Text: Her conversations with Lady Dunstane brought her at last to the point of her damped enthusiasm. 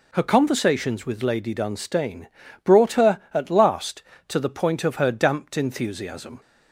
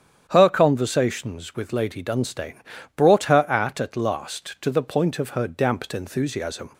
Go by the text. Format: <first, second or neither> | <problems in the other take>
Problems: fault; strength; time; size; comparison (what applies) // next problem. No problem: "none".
first | starts louder than the rest; strong; until 1.2 s; 9 dB // pauses between "Dunstane" and "brought"; slight; at 2.6 s; 0.36 s long; also in the first // says "at" twice; at 3.8 s